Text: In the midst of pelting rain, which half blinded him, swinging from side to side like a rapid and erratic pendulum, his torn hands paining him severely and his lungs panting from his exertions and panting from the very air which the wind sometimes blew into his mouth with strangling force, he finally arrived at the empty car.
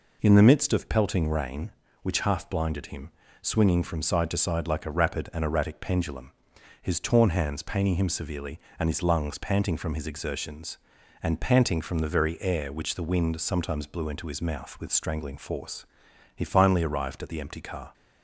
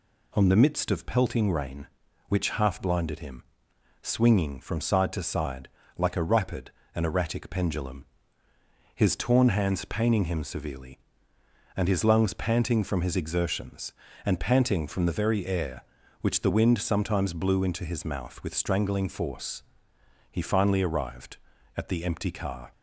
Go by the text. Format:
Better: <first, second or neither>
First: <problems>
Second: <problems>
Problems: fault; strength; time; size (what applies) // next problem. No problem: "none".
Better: first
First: none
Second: says "On" for "In"; at 0.3 s // pauses between "side" and "like"; slight; at 5.6 s; 0.30 s long